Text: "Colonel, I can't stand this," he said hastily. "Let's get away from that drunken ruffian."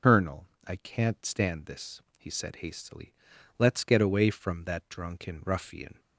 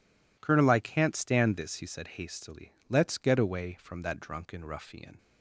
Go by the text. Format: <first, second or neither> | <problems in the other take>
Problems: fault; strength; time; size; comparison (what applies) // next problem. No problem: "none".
second | loses the start of "Colonel"; at 0.0 s; 100 ms